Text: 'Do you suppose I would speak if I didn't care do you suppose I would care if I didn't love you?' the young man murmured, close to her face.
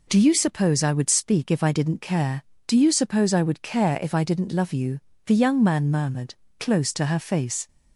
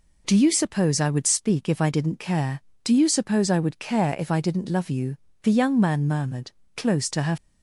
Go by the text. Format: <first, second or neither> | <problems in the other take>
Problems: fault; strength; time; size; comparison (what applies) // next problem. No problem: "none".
first | stops before "face"; at 7.3 s